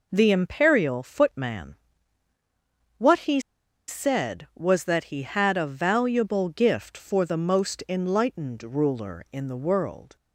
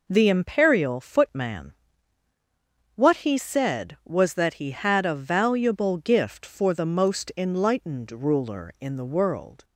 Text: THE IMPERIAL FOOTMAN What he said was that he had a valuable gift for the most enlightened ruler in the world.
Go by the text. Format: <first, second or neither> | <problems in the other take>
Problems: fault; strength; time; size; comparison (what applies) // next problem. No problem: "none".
second | pauses between "FOOTMAN" and "What"; at 1.7 s; 1.2 s long; also in the second // pauses between "he" and "said"; noticeable; at 3.3 s; 0.48 s long